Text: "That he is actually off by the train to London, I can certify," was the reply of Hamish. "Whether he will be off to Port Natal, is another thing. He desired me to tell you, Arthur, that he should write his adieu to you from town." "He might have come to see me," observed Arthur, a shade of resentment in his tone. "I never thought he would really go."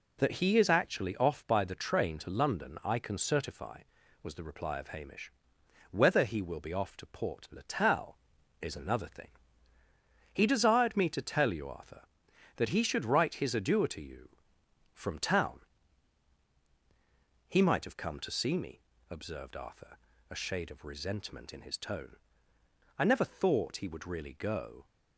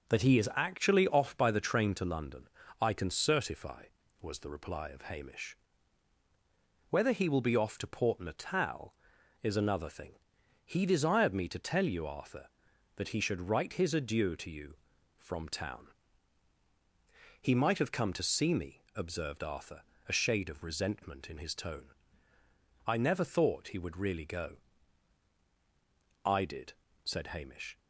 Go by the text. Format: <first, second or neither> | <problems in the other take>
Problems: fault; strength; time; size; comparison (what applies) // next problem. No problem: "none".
first | goes on to say "I did said Hamish"; from 26.2 s on; 1.5 s long